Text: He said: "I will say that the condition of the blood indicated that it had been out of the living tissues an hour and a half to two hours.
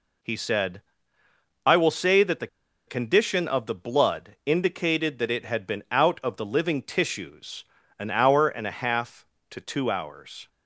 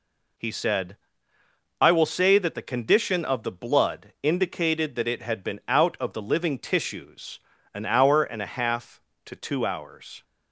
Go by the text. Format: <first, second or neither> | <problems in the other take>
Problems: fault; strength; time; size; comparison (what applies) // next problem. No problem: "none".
second | pauses between "the" and "condition"; at 2.4 s; 0.41 s long // pauses between "tissues" and "an"; slight; at 7.6 s; 0.34 s long; slight in the second